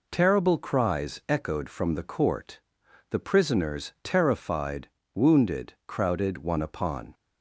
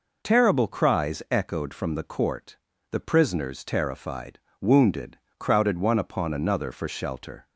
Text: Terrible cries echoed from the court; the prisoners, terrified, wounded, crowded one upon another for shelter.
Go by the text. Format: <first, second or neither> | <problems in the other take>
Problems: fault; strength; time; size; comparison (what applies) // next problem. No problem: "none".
second | stops before "another for shelter"; at 7.1 s